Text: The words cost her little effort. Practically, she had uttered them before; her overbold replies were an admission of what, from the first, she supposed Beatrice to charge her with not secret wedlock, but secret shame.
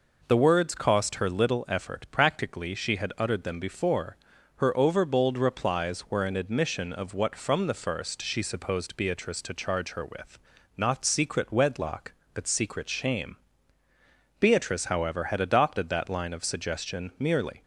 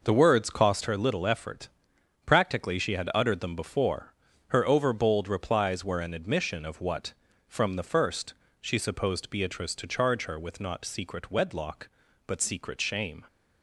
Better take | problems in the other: second | pauses between "with" and "not"; at 10.3 s; 0.38 s long // goes on to say "Beatrice however had adopted that line of suggestion merely"; strong; from 14.4 s on; 3.2 s long

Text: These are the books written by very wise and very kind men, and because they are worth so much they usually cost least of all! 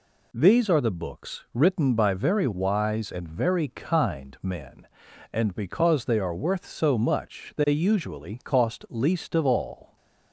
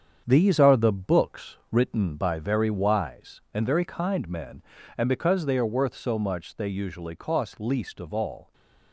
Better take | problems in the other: first | gets quieter; throughout; 7 dB

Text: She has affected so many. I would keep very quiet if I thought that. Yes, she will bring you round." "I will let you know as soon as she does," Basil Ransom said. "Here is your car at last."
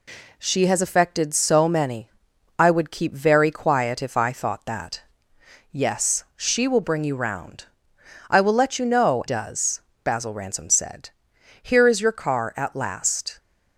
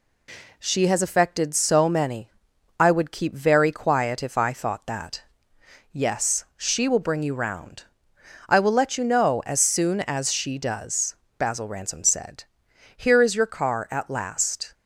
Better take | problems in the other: second | skips "as soon as she"; at 9.2 s

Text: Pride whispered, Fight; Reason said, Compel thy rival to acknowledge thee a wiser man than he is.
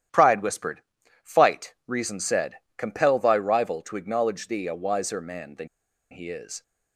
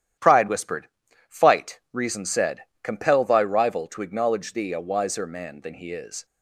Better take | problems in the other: second | starts louder than the rest; strong; until 1.5 s; 11.5 dB; strong in the second // pauses between "than" and "he"; at 5.6 s; 0.43 s long

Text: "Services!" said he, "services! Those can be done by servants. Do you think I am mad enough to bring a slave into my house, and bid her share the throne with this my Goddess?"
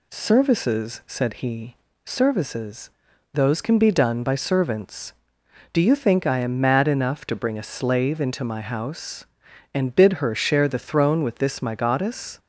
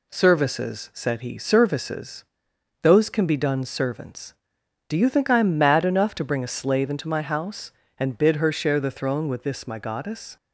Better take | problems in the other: first | skips "by"; at 3.6 s

